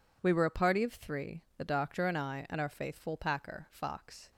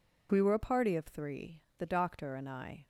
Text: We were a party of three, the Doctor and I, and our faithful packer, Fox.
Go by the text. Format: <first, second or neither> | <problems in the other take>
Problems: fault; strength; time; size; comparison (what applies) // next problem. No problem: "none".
first | stops before "and our faithful packer Fox"; at 2.8 s